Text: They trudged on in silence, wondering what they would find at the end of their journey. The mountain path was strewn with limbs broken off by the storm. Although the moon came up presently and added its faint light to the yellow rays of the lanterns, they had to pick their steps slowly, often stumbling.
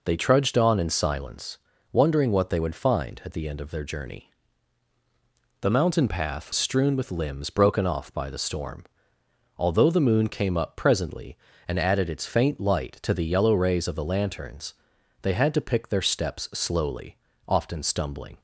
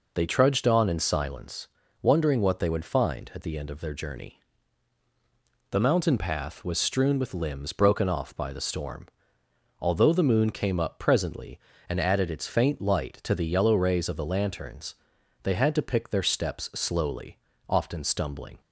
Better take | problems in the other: second | skips "was"; at 6.5 s

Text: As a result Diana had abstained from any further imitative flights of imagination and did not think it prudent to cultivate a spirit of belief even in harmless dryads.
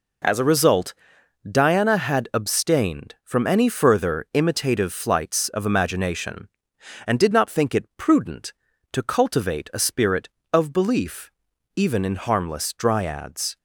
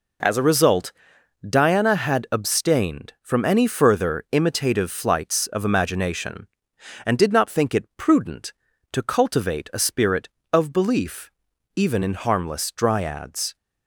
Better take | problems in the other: neither | pauses between "result" and "Diana"; noticeable; the same in both // pauses between "belief" and "even"; the same in both

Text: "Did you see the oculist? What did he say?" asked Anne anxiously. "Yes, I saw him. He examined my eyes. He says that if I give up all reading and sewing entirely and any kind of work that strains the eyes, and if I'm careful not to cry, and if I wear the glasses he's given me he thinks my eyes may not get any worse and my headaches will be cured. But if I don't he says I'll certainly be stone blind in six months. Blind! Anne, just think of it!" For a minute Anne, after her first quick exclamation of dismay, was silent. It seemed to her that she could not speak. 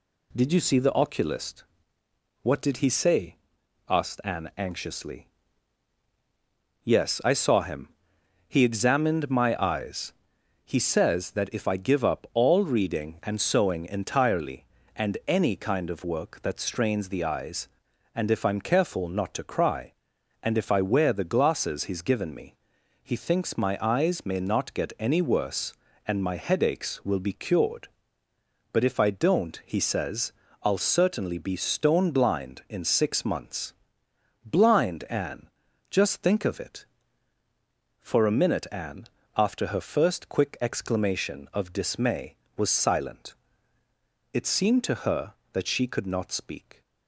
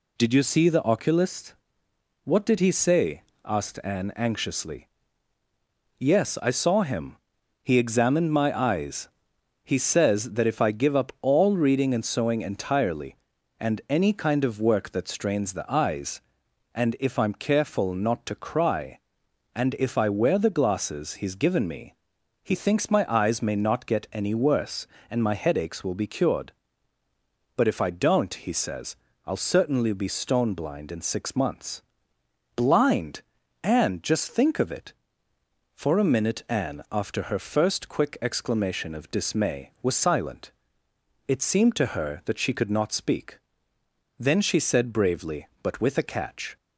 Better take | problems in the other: first | pauses between "me" and "he"; noticeable; at 21.9 s; 0.48 s long; noticeable in the first // pauses between "says" and "I'll"; slight; at 28.9 s; 0.32 s long; slight in the first // goes on to say "Then she said bravely but with a catch"; strong; from 44.1 s on; 2.4 s long

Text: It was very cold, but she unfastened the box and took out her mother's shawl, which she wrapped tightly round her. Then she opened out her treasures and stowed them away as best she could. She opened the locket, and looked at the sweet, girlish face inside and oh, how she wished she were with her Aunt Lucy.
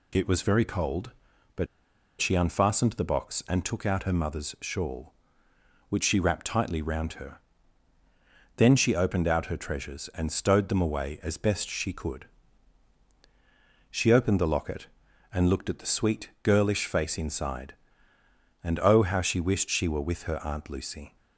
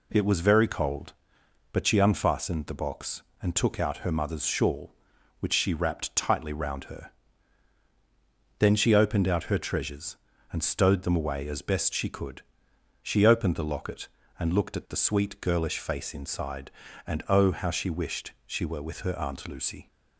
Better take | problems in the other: second | pauses between "but" and "she"; noticeable; at 1.6 s; 0.53 s long

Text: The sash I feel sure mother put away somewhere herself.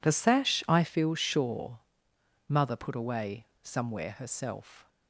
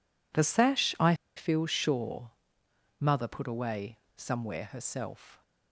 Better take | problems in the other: first | pauses between "I" and "feel"; slight; at 1.1 s; 0.22 s long // pauses between "sure" and "mother"; noticeable; at 2.3 s; 0.70 s long; noticeable in the first // pauses between "away" and "somewhere"; slight; at 3.9 s; 0.22 s long; slight in the first

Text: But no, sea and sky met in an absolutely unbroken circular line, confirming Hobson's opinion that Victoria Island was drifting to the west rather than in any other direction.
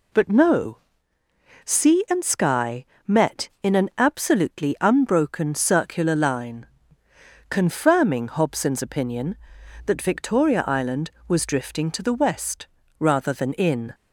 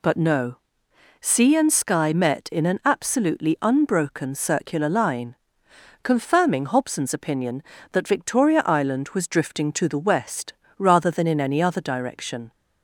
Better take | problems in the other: second | pauses between "sky" and "met"; slight; at 2.8 s; 0.22 s long // pauses between "west" and "rather"; slight; at 12.6 s; 0.32 s long; slight in the second // stops before "any other direction"; at 13.9 s

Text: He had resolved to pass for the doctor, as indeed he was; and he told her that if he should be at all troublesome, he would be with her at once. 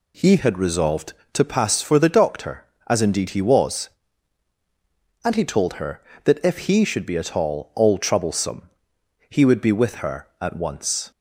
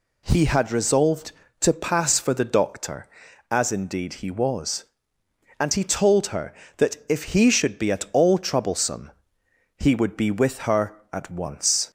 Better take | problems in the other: second | says "all" twice; at 7.7 s

